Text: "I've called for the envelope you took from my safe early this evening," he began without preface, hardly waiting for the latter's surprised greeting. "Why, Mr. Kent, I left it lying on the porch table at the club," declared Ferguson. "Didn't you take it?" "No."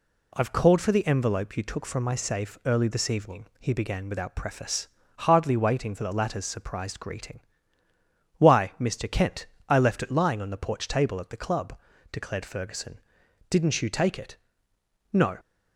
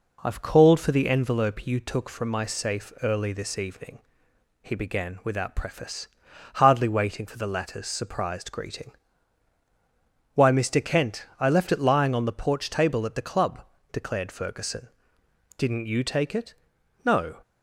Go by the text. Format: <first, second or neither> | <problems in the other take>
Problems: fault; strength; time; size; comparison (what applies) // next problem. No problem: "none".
neither | none